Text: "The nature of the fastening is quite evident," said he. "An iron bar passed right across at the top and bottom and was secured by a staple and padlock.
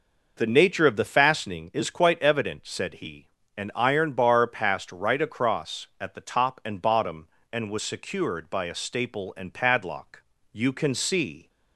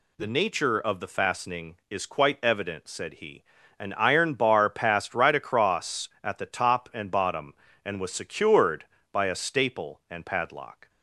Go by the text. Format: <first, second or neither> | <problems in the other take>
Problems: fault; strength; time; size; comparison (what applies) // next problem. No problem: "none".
second | goes on to say "You can see"; noticeable; from 10.5 s on; 0.96 s long